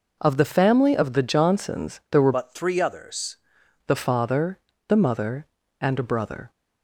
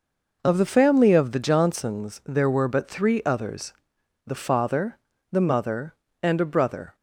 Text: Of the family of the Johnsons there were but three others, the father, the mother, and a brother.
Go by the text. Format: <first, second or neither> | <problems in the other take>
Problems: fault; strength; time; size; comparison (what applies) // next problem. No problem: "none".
second | changes voice from "but" to "others"; from 2.3 to 3.3 s; 1.0 s long